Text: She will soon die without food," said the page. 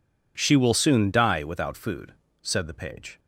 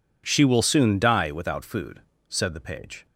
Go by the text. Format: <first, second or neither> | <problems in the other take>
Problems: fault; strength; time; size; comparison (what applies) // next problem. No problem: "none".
neither | none